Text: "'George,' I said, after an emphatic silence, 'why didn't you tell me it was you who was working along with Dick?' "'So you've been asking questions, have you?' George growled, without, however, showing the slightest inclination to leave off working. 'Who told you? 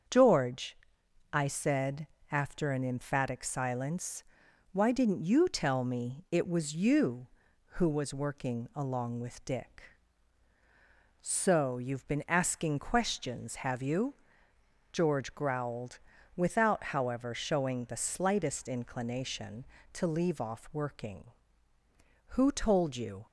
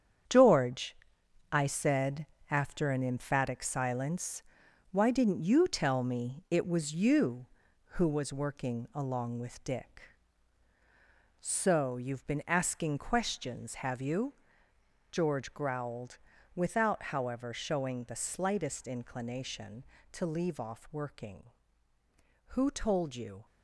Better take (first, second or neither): first